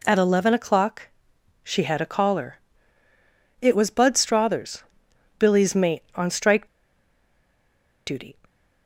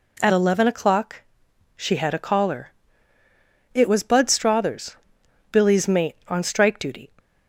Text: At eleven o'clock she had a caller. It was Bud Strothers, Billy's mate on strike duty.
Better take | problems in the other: second | pauses between "o'clock" and "she"; noticeable; at 1.0 s; 0.60 s long; noticeable in the second // pauses between "strike" and "duty"; strong; at 6.6 s; 1.4 s long

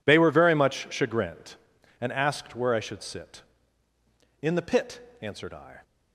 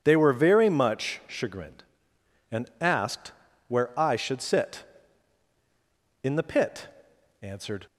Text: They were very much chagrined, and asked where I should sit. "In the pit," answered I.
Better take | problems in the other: first | pauses between "asked" and "where"; slight; at 3.3 s; 0.36 s long // stops before "I"; at 7.8 s

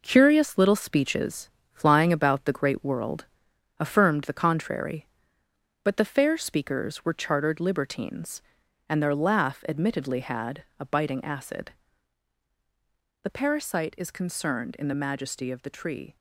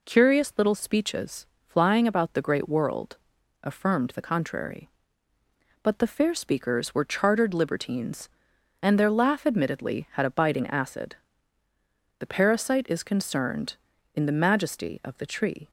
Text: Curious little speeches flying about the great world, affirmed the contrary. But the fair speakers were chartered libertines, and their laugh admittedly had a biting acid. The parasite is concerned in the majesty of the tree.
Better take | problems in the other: second | gets quieter; throughout; 7 dB // pauses between "speeches" and "flying"; slight; at 1.5 s; 0.22 s long; slight in the second

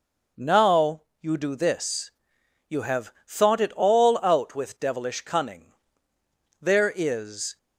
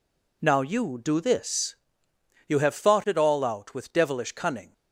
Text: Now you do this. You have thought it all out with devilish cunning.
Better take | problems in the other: second | pauses between "Now" and "you"; slight; at 1.0 s; 0.18 s long // goes on to say "There is"; noticeable; from 6.6 s on; 0.96 s long

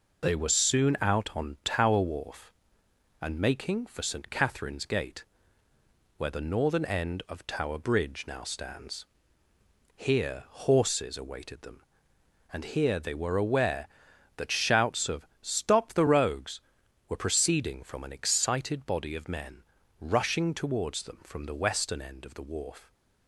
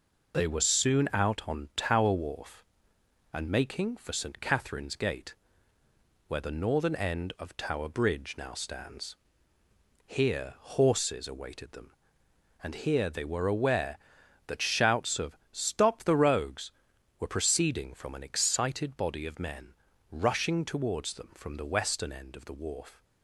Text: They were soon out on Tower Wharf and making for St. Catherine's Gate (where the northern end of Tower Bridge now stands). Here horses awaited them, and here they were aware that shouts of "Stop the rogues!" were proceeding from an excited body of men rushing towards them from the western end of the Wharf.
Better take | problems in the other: neither | pauses between "of" and "Stop"; slight; the same in both // pauses between "men" and "rushing"; slight; the same in both

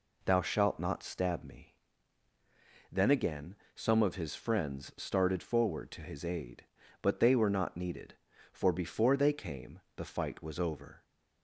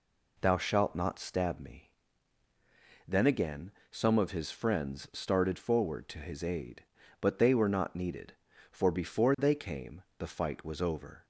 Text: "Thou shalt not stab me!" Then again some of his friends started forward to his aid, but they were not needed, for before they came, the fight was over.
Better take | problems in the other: neither | pauses between "again" and "some"; slight; the same in both

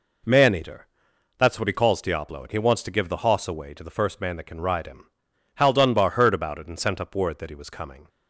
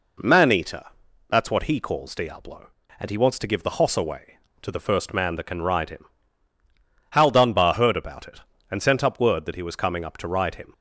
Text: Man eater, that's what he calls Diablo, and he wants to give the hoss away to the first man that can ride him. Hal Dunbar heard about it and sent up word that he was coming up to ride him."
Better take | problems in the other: second | stops before "up to ride him"; at 8.0 s

